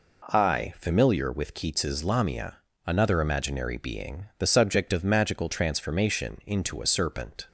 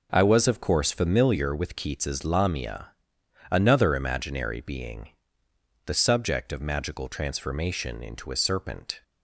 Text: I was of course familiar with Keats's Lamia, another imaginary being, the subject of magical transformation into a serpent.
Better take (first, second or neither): second